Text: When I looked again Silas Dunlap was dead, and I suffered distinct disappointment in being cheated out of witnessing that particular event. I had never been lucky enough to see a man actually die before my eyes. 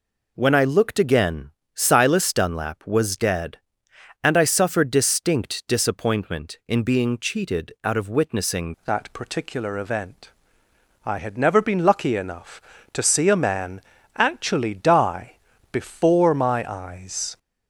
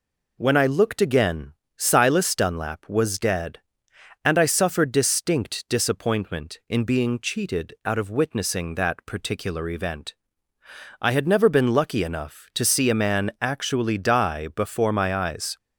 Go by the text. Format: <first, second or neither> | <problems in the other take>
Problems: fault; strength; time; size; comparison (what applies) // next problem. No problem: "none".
second | pauses between "again" and "Silas"; slight; at 1.5 s; 0.26 s long; slight in the second // changes voice at "that"; from 8.8 s on; 8.5 s long // pauses between "man" and "actually"; at 13.7 s; 0.38 s long // pauses between "die" and "before"; slight; at 15.3 s; 0.36 s long